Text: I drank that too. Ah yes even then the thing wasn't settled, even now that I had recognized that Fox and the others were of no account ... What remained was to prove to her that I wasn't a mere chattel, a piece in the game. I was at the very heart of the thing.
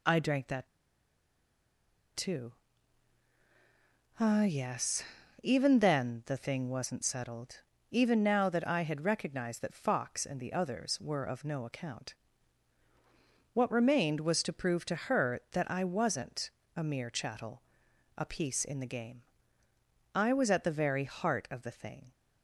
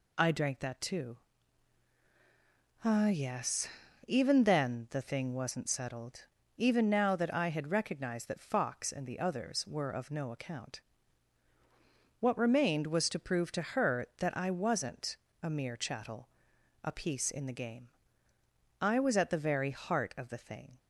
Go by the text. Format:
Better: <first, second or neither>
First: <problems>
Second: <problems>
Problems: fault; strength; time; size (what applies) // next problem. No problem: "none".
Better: second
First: pauses between "that" and "too"; strong; at 0.6 s; 1.4 s long // pauses between "yes" and "even"; at 5.0 s; 0.38 s long // pauses between "wasn't" and "a"; slight; at 16.5 s; 0.24 s long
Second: pauses between "yes" and "even"; at 3.6 s; 0.38 s long // pauses between "wasn't" and "a"; slight; at 15.1 s; 0.24 s long